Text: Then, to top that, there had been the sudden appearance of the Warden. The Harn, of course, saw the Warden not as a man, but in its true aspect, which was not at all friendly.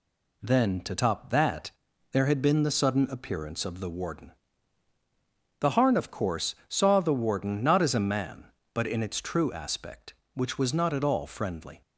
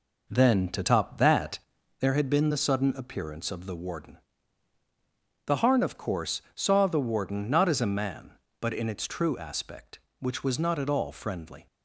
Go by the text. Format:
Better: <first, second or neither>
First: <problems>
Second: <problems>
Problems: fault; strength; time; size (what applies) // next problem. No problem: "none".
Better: first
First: none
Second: starts louder than the rest; noticeable; until 1.9 s; 4.5 dB